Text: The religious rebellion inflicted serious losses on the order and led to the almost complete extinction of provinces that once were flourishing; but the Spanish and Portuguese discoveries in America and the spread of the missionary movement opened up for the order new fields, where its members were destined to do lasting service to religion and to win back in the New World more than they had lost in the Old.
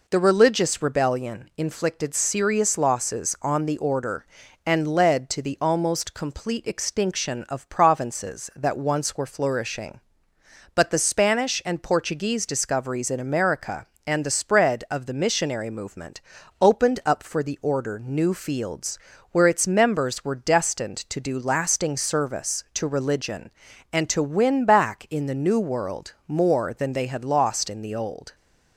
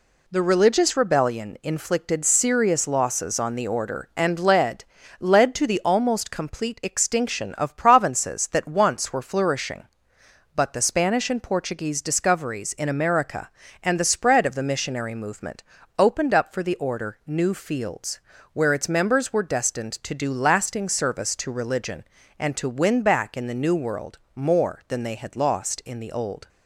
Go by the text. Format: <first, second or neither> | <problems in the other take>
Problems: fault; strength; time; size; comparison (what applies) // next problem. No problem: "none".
first | says "led" twice; at 5.2 s // pauses between "movement" and "opened"; slight; at 15.6 s; 0.34 s long; also in the first // pauses between "World" and "more"; slight; at 24.1 s; 0.16 s long; slight in the first